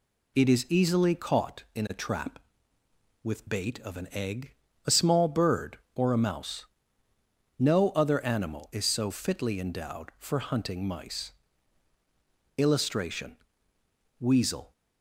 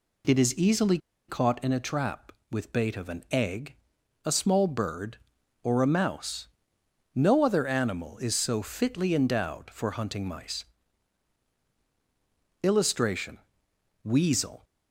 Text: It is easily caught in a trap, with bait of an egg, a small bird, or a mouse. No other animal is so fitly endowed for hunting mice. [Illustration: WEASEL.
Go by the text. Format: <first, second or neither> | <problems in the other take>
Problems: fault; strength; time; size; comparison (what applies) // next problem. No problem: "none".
first | pauses between "easily" and "caught"; slight; at 0.9 s; 0.30 s long